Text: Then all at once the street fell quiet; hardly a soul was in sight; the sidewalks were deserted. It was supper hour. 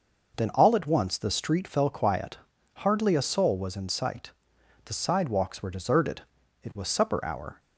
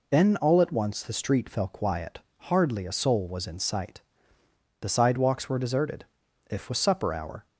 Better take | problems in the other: first | says "If" for "It"; at 6.4 s

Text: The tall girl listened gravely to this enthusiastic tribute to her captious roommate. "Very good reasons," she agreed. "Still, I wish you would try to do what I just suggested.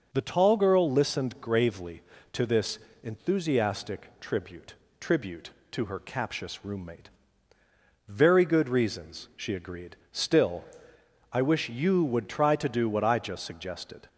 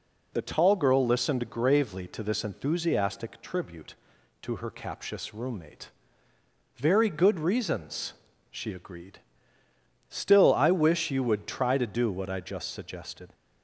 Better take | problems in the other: second | pauses between "this" and "enthusiastic"; slight; at 2.7 s; 0.24 s long // says "tribute" twice; at 4.9 s

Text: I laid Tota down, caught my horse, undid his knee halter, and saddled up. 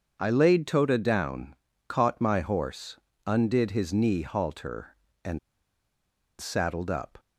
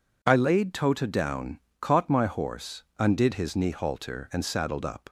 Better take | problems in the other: second | starts louder than the rest; until 1.2 s; 7 dB // pauses between "and" and "saddled"; at 5.3 s; 1.0 s long

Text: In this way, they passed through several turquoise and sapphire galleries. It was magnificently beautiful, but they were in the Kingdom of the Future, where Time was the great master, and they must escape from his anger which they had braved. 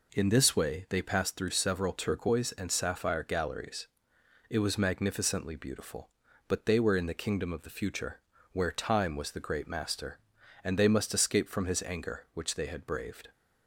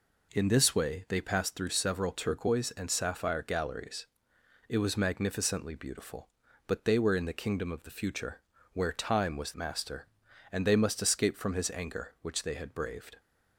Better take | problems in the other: first | skips "the great"; at 9.5 s

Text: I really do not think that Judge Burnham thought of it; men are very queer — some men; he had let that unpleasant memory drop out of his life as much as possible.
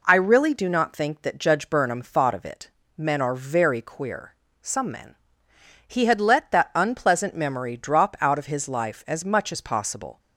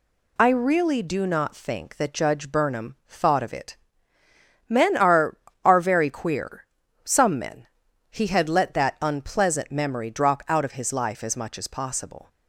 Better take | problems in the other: first | says "are" twice; at 5.6 s

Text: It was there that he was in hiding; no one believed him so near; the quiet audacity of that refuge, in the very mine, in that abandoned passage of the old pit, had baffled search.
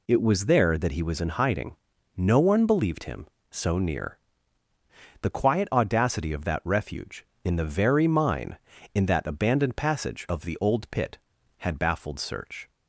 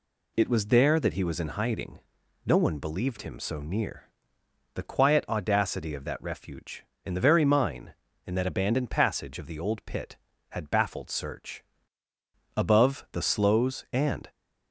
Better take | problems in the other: first | goes on to say "Above the sloes and"; strong; from 12.5 s on; 1.7 s long

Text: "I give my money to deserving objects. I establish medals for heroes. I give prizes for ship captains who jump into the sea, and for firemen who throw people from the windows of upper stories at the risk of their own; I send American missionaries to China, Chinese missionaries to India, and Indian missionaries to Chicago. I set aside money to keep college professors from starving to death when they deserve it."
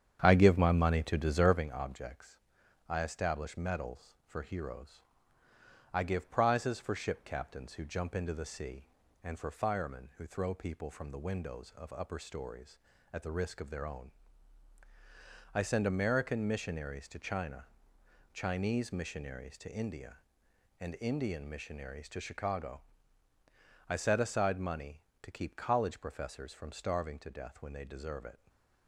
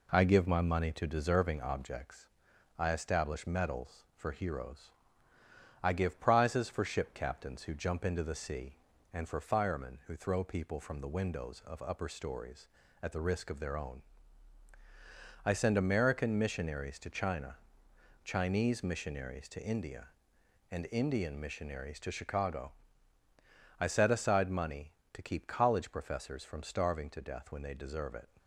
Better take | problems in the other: second | starts louder than the rest; strong; until 1.6 s; 9 dB // stays silent after the last word; slight; from 28.3 s on; 0.5 s long

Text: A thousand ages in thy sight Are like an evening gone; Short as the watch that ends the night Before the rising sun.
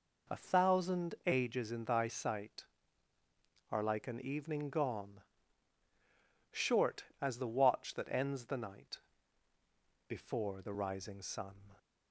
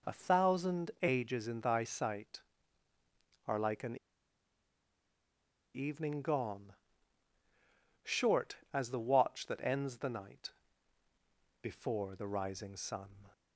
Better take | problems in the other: first | pauses between "an" and "evening"; strong; at 3.9 s; 1.7 s long // pauses between "night" and "Before"; at 10.5 s; 1.1 s long; also in the first

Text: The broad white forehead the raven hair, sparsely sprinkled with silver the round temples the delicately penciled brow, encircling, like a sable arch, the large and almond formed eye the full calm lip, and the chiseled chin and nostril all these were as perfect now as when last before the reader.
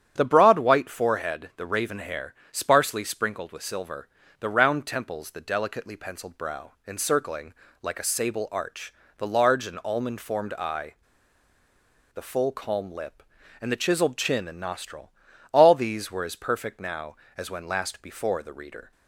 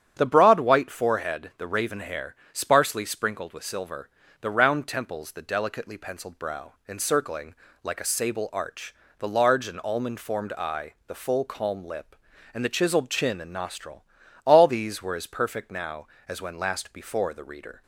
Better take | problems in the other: second | starts louder than the rest; strong; until 1.1 s; 9.5 dB; strong in the second // pauses between "silver" and "the"; slight; at 4.0 s; 0.30 s long; slight in the second // pauses between "eye" and "the"; at 10.9 s; 1.2 s long // pauses between "nostril" and "all"; at 15.1 s; 0.40 s long; also in the second

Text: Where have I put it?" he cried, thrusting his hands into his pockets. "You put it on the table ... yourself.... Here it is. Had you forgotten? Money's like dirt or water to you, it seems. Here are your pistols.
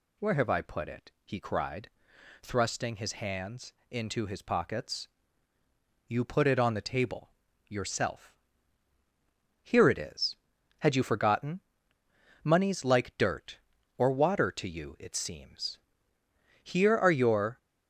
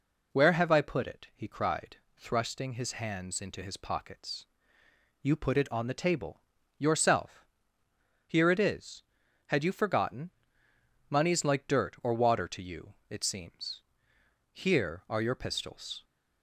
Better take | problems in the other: second | pauses between "hands" and "into"; slight; at 3.7 s; 0.16 s long // stops before "pistols"; at 17.5 s

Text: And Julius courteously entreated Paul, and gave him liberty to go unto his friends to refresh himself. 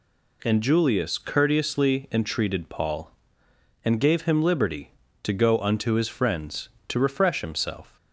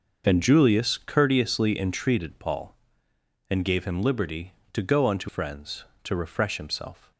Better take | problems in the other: first | skips "his"; at 5.2 s

